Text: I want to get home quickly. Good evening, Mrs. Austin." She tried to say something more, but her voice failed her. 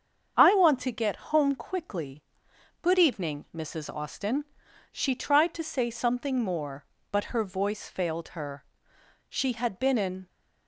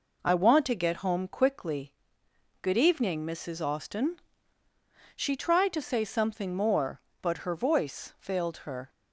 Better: second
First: starts louder than the rest; strong; until 1.3 s; 7 dB // goes on to say "She had been in"; noticeable; from 9.2 s on; 0.98 s long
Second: none

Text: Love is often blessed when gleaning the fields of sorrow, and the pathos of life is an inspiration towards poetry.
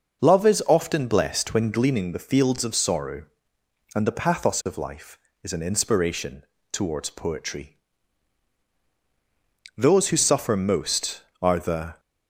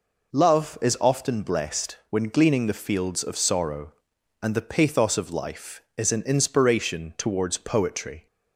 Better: second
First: pauses between "inspiration" and "towards"; slight; at 6.4 s; 0.30 s long // goes on to say "Those who suffer most are the"; strong; from 9.7 s on; 2.2 s long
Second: none

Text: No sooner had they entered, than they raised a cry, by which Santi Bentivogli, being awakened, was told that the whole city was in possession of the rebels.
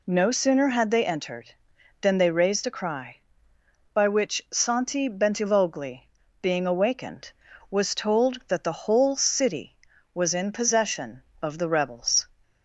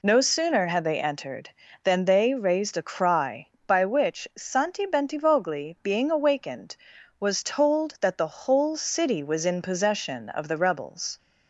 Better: neither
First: none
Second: none

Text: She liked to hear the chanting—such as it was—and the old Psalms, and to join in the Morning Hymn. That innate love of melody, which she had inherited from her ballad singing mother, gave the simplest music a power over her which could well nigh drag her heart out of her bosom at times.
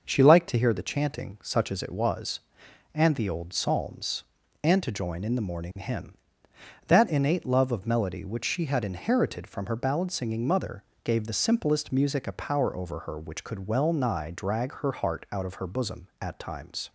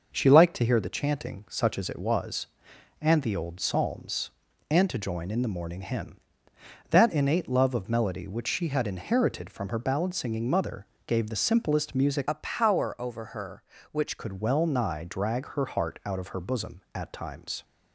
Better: first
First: none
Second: changes voice from "a" to "which"; from 12.2 to 14.1 s; 1.9 s long

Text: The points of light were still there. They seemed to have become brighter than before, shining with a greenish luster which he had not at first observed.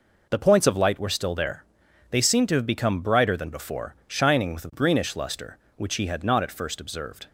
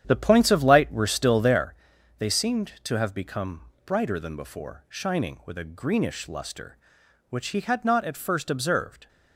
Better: first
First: none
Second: starts louder than the rest; strong; until 1.7 s; 9.5 dB // pauses between "become" and "brighter"; slight; at 3.6 s; 0.24 s long

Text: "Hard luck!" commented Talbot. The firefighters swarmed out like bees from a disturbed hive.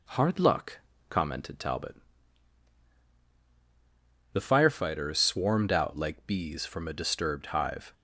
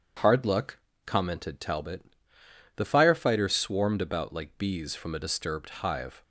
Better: first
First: none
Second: starts louder than the rest; strong; until 1.4 s; 8 dB // says "about" for "out"; at 4.0 s

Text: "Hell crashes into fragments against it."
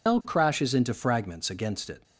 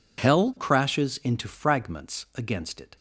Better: second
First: loses the start of "Hell"; at 0.0 s; 110 ms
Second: none

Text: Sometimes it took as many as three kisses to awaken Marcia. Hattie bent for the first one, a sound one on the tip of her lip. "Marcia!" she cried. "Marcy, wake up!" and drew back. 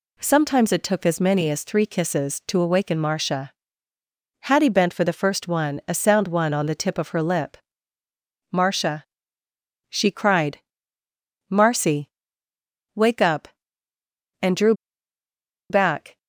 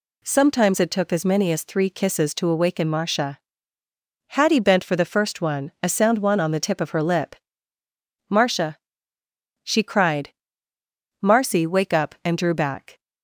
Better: second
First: pauses between "drew" and "back"; noticeable; at 14.7 s; 0.96 s long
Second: none

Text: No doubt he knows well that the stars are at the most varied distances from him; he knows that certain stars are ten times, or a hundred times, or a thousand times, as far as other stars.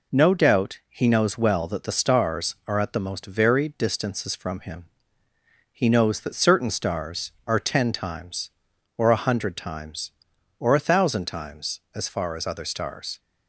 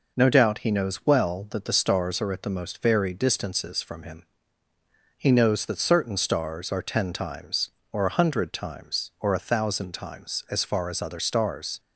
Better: neither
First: none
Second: none

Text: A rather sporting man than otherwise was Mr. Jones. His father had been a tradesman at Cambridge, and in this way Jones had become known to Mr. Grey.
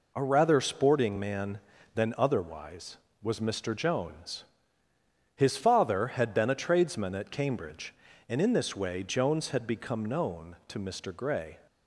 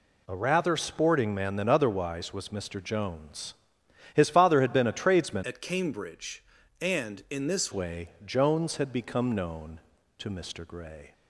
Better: first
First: none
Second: changes voice from "at" to "this"; from 5.4 to 7.7 s; 2.3 s long // pauses between "way" and "Jones"; slight; at 8.1 s; 0.16 s long

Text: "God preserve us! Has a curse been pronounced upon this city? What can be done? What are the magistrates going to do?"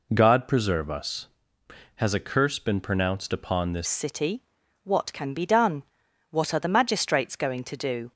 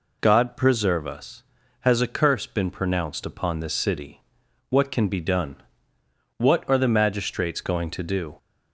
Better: second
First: changes voice at "city"; from 3.8 s on; 4.3 s long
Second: none

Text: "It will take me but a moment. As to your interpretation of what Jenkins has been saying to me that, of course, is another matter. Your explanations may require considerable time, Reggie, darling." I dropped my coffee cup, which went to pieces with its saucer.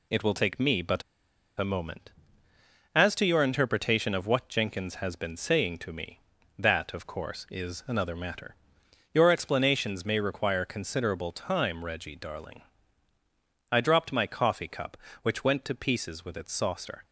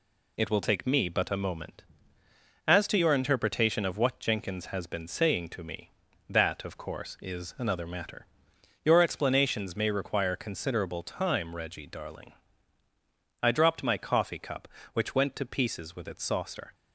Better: second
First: pauses between "but" and "a"; noticeable; at 1.0 s; 0.56 s long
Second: none

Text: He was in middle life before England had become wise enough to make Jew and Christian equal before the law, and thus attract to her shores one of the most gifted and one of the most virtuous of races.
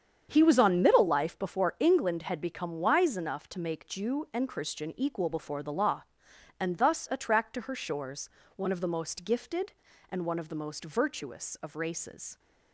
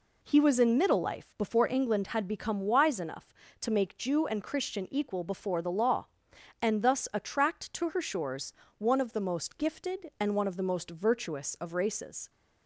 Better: second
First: starts louder than the rest; strong; until 1.3 s; 8 dB // says "on" for "in"; at 0.5 s // pauses between "shores" and "one"; slight; at 8.2 s; 0.24 s long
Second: pauses between "shores" and "one"; slight; at 8.5 s; 0.26 s long

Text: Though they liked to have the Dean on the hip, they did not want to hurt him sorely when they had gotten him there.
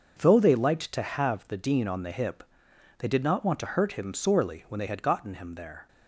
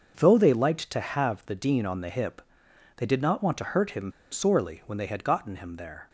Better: first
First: starts louder than the rest; until 1.2 s; 6.5 dB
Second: starts louder than the rest; until 1.2 s; 6.5 dB // pauses between "him" and "sorely"; slight; at 4.1 s; 0.21 s long

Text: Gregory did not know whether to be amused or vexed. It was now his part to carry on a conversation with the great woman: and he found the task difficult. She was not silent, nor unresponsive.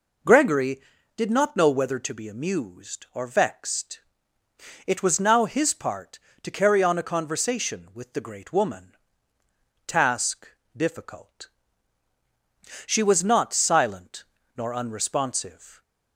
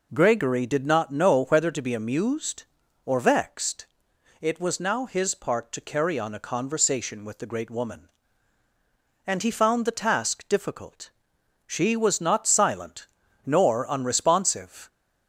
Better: second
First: skips "and he found the"; at 9.4 s // pauses between "task" and "difficult"; slight; at 10.4 s; 0.28 s long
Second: none

